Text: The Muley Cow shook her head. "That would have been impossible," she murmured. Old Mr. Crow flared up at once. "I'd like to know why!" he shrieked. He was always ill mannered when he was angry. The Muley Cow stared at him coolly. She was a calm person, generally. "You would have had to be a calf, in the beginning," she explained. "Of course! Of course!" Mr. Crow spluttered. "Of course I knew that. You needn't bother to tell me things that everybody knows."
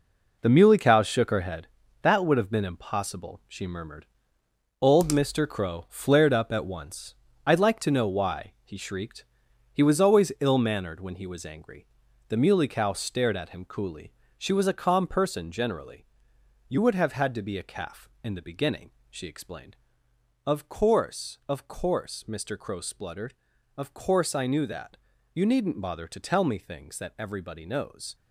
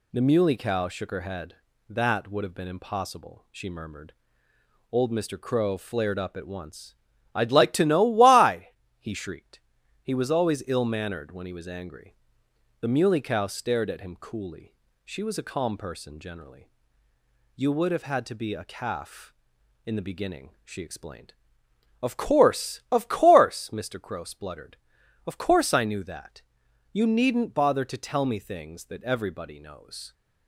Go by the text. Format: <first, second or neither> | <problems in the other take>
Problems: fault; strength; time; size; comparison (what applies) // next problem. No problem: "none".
second | gets quieter; strong; throughout; 9 dB